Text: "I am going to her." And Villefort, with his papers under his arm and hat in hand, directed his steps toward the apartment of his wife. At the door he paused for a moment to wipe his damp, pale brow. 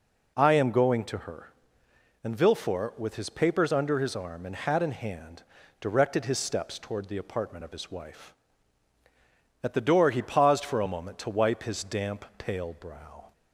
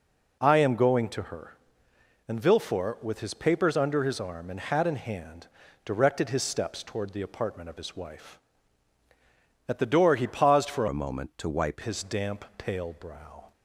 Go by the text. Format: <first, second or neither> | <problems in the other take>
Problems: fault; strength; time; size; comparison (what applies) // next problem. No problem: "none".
first | changes voice from "a" to "wipe"; from 10.8 to 11.8 s; 1.0 s long